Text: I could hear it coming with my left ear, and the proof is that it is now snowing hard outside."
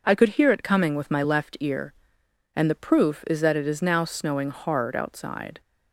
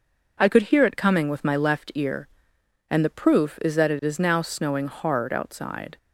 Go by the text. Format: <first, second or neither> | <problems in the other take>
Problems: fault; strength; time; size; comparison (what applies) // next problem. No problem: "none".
neither | none